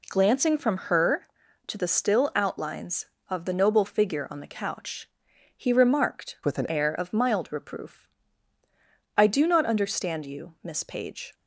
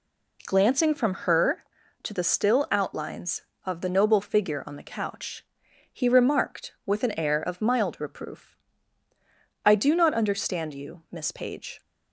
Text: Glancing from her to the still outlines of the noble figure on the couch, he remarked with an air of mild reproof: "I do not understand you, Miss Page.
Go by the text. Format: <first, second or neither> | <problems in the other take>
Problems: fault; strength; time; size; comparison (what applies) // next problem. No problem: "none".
second | changes voice from "with" to "an"; from 6.4 to 6.7 s; 0.3 s long